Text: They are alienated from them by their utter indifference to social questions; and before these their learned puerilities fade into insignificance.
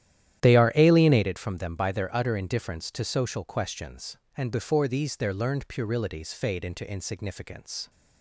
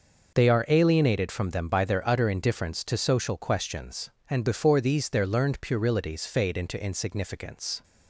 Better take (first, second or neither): second